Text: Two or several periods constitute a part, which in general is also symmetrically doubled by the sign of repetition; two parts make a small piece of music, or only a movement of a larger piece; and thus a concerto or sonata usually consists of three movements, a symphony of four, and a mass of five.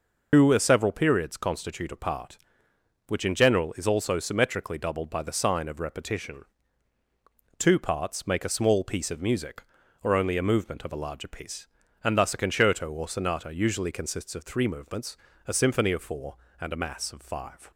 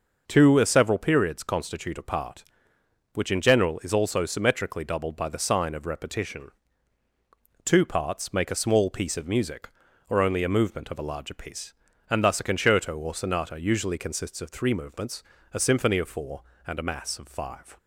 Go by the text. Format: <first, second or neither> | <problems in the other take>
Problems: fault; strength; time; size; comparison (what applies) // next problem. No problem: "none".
second | loses the start of "Two"; at 0.3 s; 120 ms